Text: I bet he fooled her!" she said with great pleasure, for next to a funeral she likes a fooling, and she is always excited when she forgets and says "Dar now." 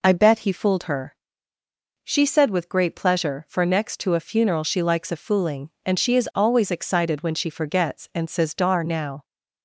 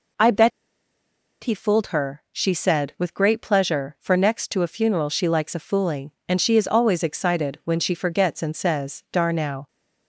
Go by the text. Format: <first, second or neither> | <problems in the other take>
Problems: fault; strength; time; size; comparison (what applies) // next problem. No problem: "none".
first | pauses between "bet" and "he"; noticeable; at 0.5 s; 0.92 s long